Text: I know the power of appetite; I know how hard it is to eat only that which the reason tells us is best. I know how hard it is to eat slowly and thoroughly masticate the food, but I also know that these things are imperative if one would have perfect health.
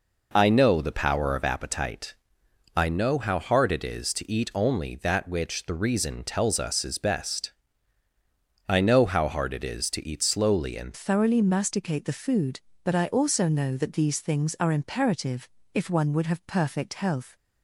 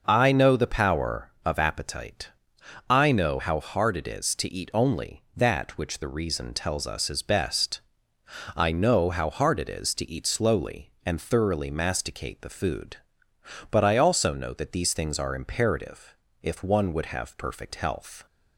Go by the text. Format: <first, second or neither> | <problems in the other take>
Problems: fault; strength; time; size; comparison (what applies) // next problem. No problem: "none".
second | changes voice at "thoroughly"; from 10.9 s on; 6.4 s long // pauses between "imperative" and "if"; slight; at 15.4 s; 0.24 s long; slight in the second